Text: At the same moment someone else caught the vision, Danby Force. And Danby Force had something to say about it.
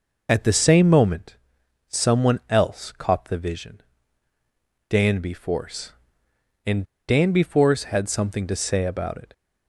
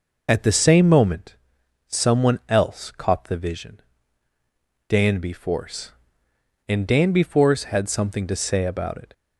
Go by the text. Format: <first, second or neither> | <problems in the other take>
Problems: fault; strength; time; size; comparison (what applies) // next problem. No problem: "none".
second | pauses between "moment" and "someone"; noticeable; at 1.3 s; 0.50 s long; noticeable in the second // pauses between "And" and "Danby"; slight; at 6.8 s; 0.24 s long